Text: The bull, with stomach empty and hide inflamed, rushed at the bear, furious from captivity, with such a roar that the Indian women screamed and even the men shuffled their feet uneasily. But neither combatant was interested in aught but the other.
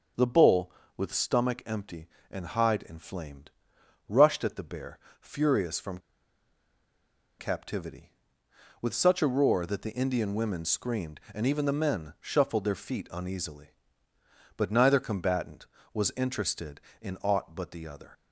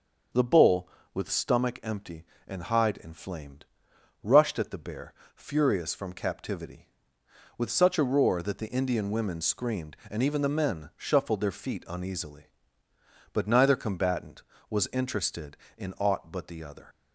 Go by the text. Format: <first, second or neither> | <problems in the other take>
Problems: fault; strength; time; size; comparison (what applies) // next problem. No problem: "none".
second | starts louder than the rest; until 1.4 s; 6.5 dB; also in the second // pauses between "from" and "captivity"; strong; at 5.9 s; 1.4 s long